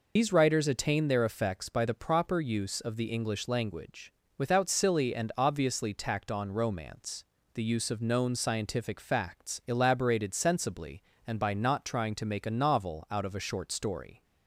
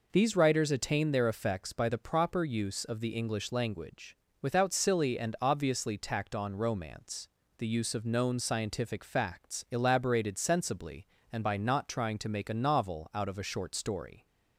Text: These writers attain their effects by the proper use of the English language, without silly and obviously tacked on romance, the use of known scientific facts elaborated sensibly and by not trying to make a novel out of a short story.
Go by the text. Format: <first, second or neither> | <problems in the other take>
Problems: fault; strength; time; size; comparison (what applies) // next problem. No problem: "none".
second | loses the start of "These"; at 0.1 s; 70 ms